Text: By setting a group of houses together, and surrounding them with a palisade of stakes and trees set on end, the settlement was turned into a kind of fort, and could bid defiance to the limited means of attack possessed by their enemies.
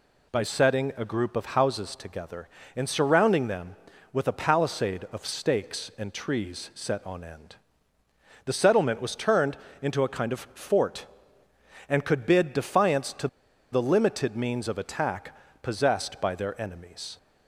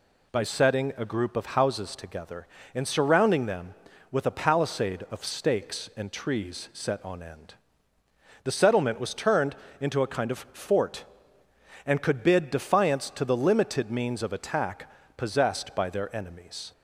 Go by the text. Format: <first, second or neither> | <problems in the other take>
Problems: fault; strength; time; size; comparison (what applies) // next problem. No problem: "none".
second | pauses between "turned" and "into"; slight; at 9.5 s; 0.24 s long; slight in the second // pauses between "to" and "the"; at 13.2 s; 0.45 s long // pauses between "attack" and "possessed"; slight; at 15.3 s; 0.26 s long; slight in the second